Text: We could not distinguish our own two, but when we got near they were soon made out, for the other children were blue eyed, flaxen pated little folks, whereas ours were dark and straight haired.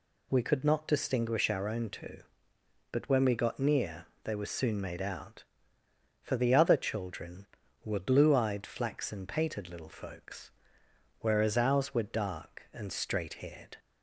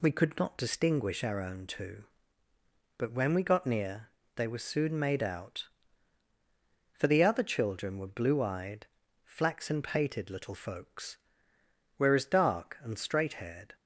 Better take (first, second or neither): first